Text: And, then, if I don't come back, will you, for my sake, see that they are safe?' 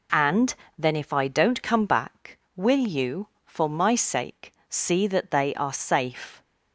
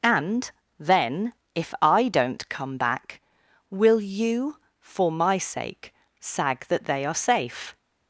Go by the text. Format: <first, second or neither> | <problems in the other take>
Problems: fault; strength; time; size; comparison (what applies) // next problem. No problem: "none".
first | says "sag" for "see"; at 6.1 s